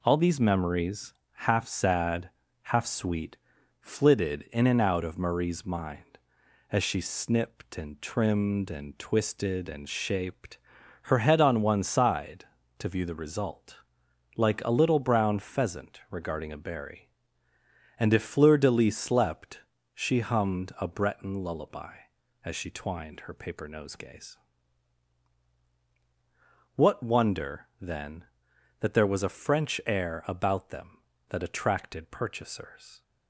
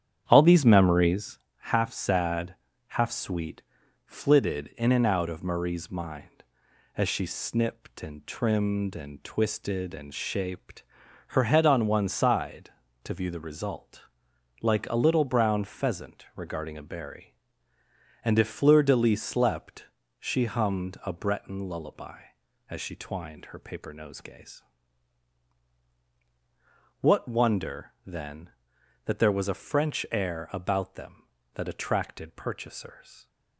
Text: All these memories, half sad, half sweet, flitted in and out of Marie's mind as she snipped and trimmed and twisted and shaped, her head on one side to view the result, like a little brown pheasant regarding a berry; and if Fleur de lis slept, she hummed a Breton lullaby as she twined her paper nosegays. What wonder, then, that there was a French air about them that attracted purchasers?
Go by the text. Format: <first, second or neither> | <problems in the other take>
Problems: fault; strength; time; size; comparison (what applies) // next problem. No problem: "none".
first | starts louder than the rest; strong; until 1.3 s; 9 dB